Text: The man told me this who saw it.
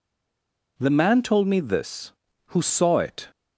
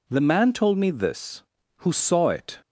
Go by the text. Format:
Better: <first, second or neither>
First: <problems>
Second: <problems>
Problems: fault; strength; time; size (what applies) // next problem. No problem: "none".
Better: second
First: stays silent before the first word; slight; until 0.7 s; 0.7 s long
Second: none